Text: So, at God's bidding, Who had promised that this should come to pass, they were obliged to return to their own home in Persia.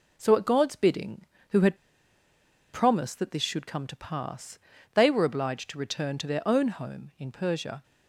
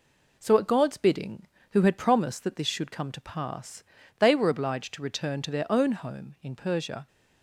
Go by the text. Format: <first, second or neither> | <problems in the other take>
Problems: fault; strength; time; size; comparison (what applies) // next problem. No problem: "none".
second | pauses between "had" and "promised"; noticeable; at 1.7 s; 0.97 s long